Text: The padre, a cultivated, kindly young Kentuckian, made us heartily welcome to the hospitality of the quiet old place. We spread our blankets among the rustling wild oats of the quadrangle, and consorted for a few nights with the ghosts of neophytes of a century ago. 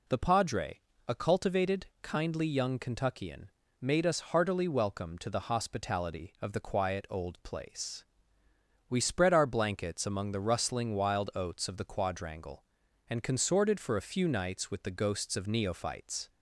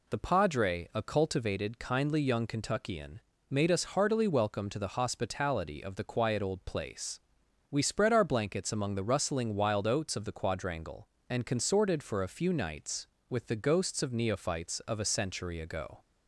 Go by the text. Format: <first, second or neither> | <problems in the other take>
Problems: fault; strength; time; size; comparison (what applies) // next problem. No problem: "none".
second | stops before "of a century ago"; at 16.2 s